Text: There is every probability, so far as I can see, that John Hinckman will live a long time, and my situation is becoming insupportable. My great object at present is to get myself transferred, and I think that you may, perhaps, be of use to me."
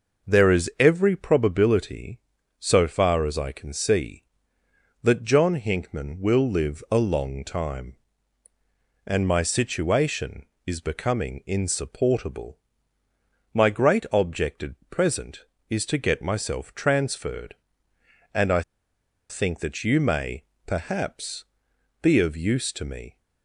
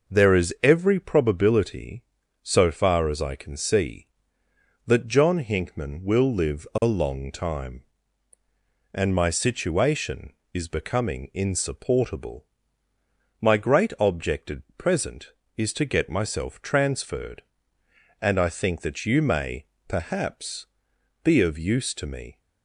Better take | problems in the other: second | pauses between "I" and "think"; noticeable; at 18.6 s; 0.68 s long

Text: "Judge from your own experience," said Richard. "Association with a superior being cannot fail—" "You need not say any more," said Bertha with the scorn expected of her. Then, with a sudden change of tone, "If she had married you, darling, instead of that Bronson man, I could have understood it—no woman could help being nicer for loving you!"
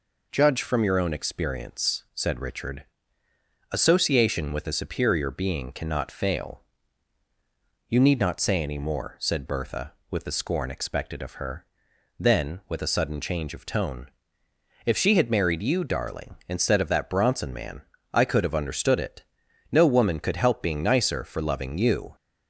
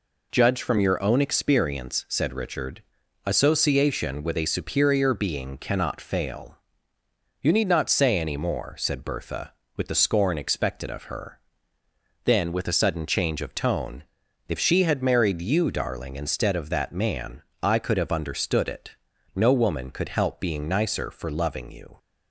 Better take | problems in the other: first | skips "Bronson"; at 16.9 s

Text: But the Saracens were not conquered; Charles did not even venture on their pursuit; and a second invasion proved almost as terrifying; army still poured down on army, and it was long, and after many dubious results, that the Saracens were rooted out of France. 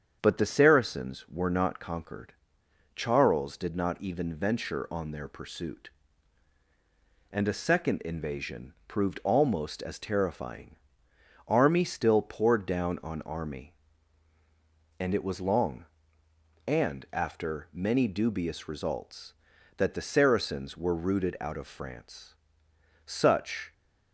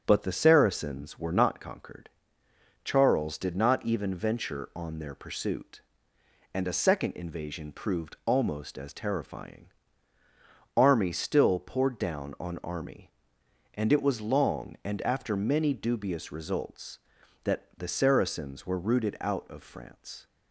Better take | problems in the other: second | starts louder than the rest; strong; until 1.2 s; 7.5 dB; strong in the second // goes on to say "Such"; noticeable; from 23.0 s on; 0.66 s long

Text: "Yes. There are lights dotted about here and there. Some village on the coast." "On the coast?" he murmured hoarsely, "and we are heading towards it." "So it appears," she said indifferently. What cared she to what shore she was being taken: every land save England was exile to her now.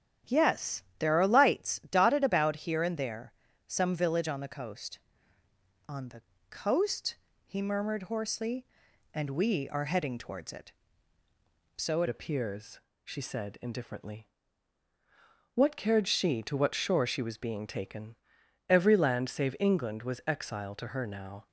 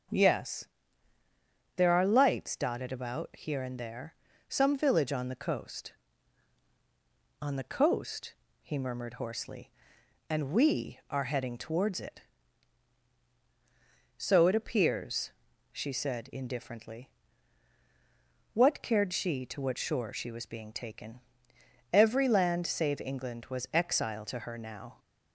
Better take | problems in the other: second | starts louder than the rest; strong; until 1.4 s; 9.5 dB; also in the second // pauses between "the" and "coast"; slight; at 6.2 s; 0.28 s long // changes voice at "appears"; from 12.0 s on; 9.4 s long

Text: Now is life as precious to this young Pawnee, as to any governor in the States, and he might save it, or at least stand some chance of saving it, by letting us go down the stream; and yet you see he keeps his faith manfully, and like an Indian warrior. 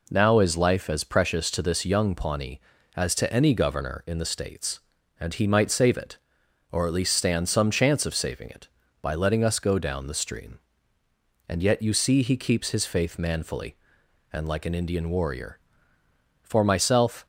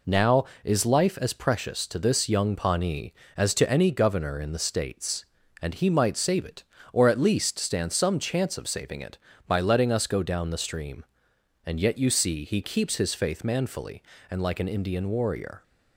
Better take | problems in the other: second | goes on to say "For myself"; noticeable; from 16.4 s on; 0.84 s long

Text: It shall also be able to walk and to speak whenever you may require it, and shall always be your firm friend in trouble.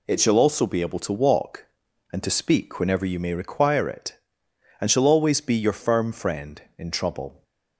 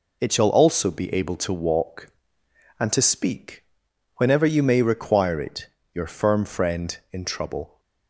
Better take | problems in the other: first | pauses between "speak" and "whenever"; noticeable; at 3.6 s; 0.52 s long // skips "and shall always be"; at 5.8 s

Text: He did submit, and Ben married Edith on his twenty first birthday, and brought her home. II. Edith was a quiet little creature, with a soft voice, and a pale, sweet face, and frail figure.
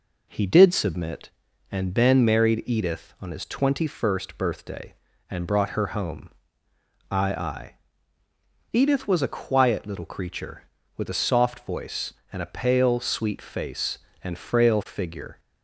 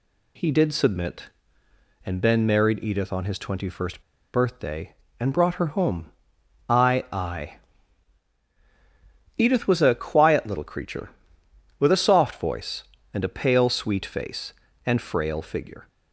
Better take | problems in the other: first | pauses between "first" and "birthday"; slight; at 4.0 s; 0.31 s long

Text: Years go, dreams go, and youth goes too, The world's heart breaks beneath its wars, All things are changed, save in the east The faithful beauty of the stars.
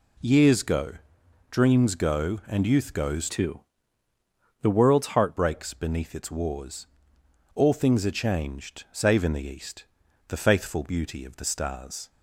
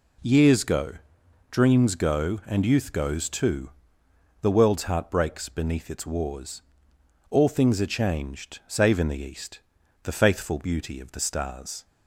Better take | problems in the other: second | changes voice from "too" to "heart"; from 3.2 to 5.3 s; 2.1 s long // pauses between "east" and "The"; at 9.8 s; 0.44 s long; also in the second

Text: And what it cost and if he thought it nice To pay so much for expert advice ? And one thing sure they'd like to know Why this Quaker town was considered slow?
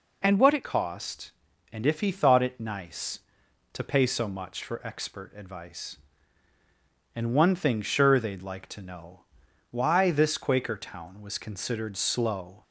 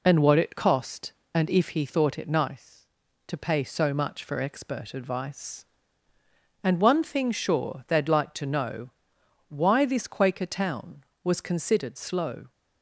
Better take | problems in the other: second | changes voice at "cost"; from 0.6 s on; 12.0 s long // pauses between "know" and "Why"; noticeable; at 9.2 s; 0.50 s long; noticeable in the second

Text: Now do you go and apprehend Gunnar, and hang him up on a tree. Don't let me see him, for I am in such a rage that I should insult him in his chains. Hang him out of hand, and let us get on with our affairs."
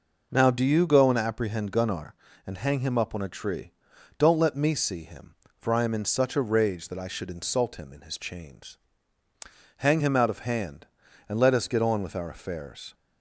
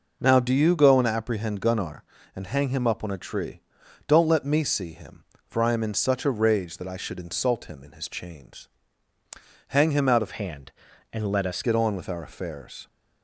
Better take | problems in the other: first | changes voice from "hand" to "us"; from 10.3 to 11.6 s; 1.3 s long

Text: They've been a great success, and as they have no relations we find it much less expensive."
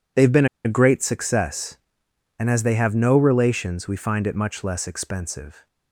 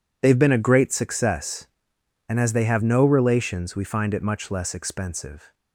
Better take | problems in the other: second | pauses between "been" and "a"; slight; at 0.4 s; 0.18 s long

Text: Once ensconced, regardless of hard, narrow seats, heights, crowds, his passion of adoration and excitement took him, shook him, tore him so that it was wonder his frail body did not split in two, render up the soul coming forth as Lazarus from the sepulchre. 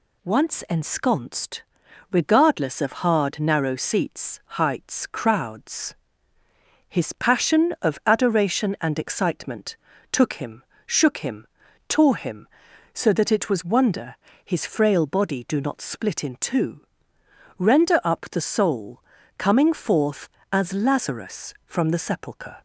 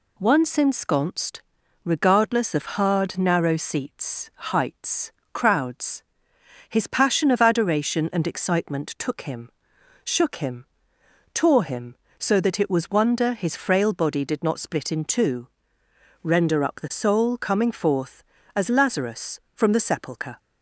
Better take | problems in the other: second | pauses between "excitement" and "took"; slight; at 9.7 s; 0.34 s long // pauses between "wonder" and "his"; slight; at 14.1 s; 0.26 s long // says "do" for "did"; at 15.4 s // pauses between "soul" and "coming"; at 18.9 s; 0.38 s long

